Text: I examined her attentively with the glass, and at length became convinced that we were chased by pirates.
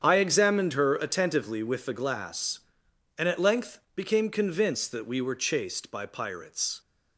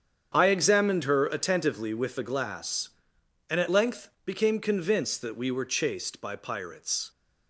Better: neither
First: starts louder than the rest; strong; until 1.0 s; 8 dB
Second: starts louder than the rest; strong; until 1.3 s; 8 dB

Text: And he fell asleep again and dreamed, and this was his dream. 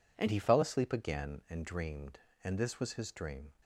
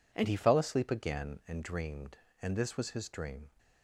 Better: neither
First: none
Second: none

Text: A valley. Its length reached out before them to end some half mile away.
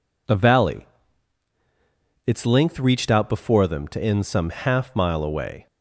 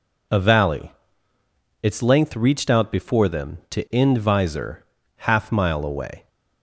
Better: first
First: none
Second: says "visor" for "some"; at 4.1 s

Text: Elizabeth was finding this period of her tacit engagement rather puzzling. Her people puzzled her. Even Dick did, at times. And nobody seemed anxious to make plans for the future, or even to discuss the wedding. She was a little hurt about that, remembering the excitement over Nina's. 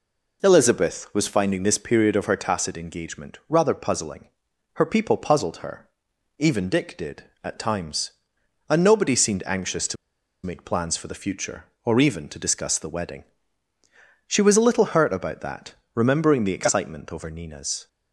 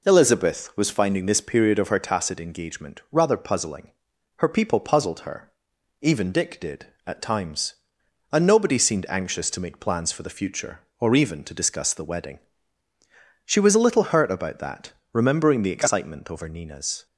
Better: second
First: pauses between "to" and "make"; noticeable; at 9.9 s; 0.49 s long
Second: none

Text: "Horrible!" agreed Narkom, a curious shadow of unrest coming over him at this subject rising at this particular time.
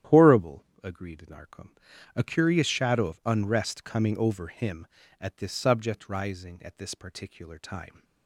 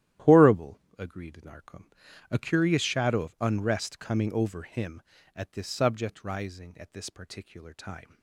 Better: first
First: starts louder than the rest; strong; until 1.3 s; 11 dB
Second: gets quieter; strong; throughout; 12.5 dB // starts louder than the rest; strong; until 1.4 s; 12.5 dB

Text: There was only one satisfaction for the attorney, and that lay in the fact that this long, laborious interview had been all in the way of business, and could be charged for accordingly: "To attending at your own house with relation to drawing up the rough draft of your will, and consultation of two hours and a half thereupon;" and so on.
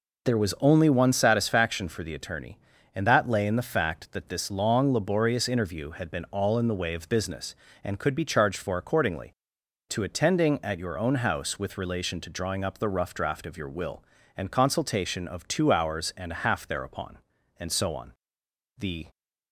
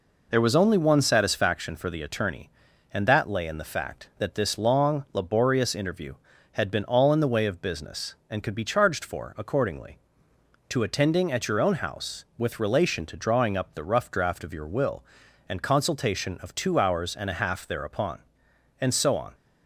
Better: second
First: goes on to say "The"; slight; from 18.7 s on; 0.30 s long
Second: none

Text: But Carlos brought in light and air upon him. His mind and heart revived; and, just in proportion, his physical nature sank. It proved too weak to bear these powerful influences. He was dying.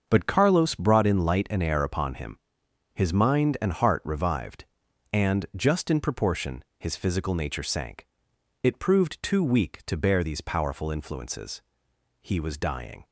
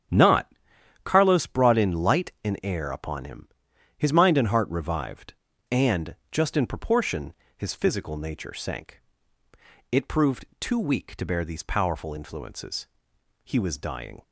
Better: first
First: starts louder than the rest; until 1.1 s; 7 dB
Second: starts louder than the rest; strong; until 1.6 s; 9 dB // says "Not" for "But"; at 0.0 s

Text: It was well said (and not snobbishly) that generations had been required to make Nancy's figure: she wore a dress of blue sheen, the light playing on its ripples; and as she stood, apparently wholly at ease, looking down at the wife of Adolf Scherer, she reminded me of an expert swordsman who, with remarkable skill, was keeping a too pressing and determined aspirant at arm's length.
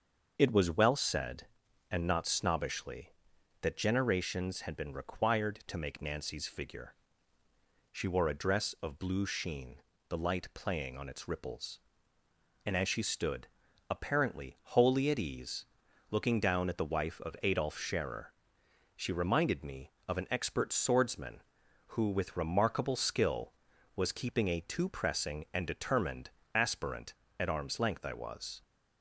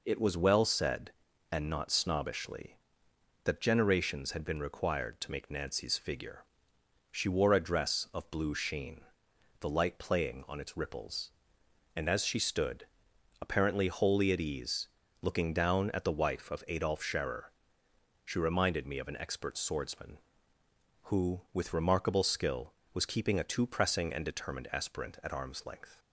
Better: second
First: starts louder than the rest; until 1.3 s; 6.5 dB // pauses between "determined" and "aspirant"; slight; at 26.3 s; 0.24 s long // goes on to say "I was"; from 28.0 s on; 0.60 s long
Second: none

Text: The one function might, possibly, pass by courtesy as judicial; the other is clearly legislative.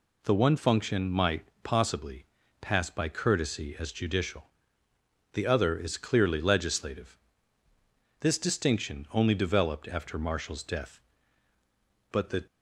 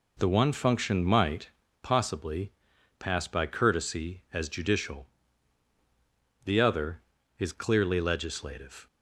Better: second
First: goes on to say "This distinction only developed after Marshall's death but the"; strong; from 8.2 s on; 4.2 s long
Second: none

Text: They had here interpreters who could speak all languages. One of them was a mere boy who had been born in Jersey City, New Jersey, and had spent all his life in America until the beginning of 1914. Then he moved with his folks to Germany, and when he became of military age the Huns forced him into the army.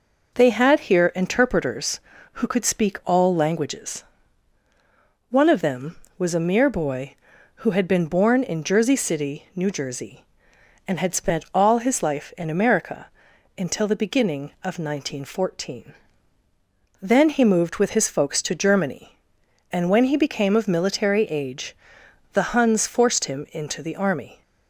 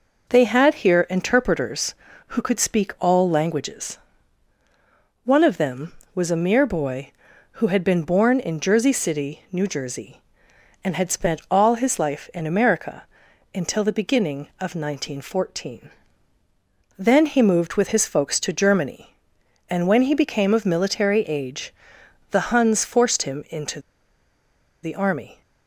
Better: first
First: pauses between "America" and "until"; noticeable; at 13.0 s; 0.48 s long // pauses between "age" and "the"; noticeable; at 21.7 s; 0.58 s long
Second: pauses between "America" and "until"; noticeable; at 13.0 s; 0.48 s long // pauses between "age" and "the"; noticeable; at 21.7 s; 0.58 s long // pauses between "into" and "the"; at 23.7 s; 1.0 s long

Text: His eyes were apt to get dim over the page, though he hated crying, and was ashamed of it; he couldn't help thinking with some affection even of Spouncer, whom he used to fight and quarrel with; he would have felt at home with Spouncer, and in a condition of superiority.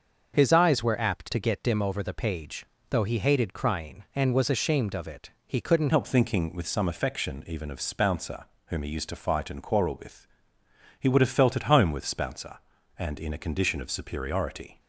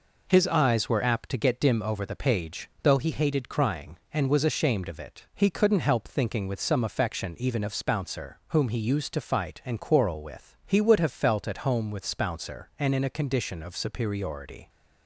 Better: second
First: starts louder than the rest; until 1.3 s; 6.5 dB // changes voice at "help"; from 5.9 s on; 8.8 s long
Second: none

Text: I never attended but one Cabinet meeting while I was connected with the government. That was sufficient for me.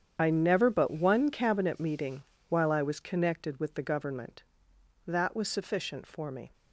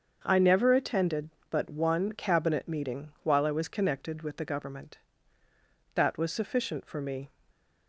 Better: second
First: starts louder than the rest; strong; until 1.1 s; 8.5 dB // skips "attended"; at 0.6 s // pauses between "meeting" and "while"; slight; at 2.2 s; 0.26 s long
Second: starts louder than the rest; until 1.2 s; 6.5 dB

